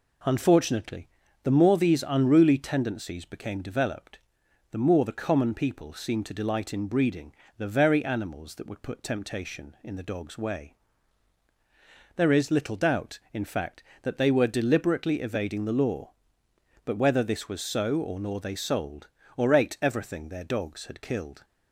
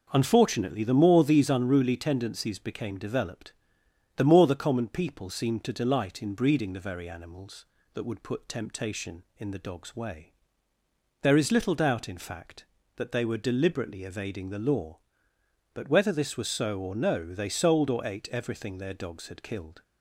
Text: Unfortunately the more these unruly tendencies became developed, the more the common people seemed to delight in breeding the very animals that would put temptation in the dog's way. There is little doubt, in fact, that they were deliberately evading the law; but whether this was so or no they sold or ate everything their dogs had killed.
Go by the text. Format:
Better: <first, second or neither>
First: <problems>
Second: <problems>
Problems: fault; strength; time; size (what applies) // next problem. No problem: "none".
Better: second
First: pauses between "Unfortunately" and "the"; slight; at 1.0 s; 0.36 s long // pauses between "breeding" and "the"; slight; at 7.3 s; 0.24 s long // says "nor" for "no"; at 18.1 s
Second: none